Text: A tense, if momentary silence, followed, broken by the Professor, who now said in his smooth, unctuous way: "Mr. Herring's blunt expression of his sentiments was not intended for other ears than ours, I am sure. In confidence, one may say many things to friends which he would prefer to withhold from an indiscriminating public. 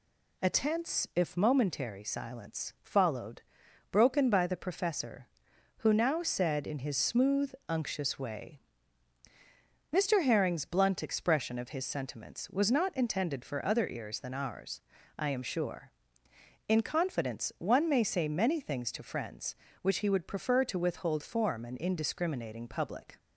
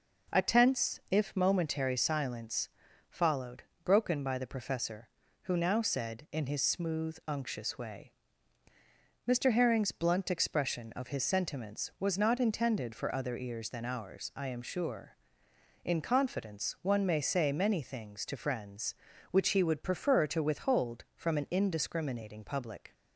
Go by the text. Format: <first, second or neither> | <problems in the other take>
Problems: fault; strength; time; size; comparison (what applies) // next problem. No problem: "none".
second | says "form" for "from"; at 21.2 s